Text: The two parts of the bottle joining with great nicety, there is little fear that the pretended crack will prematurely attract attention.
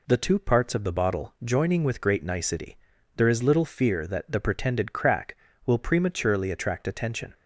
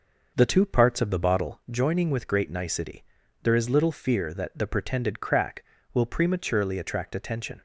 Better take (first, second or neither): first